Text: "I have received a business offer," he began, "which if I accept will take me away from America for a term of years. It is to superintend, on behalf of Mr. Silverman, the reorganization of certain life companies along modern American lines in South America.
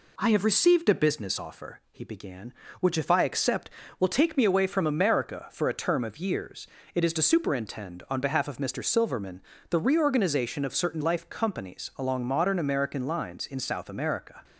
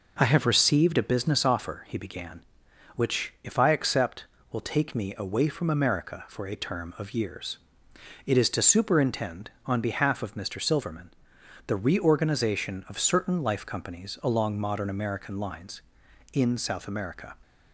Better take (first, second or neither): neither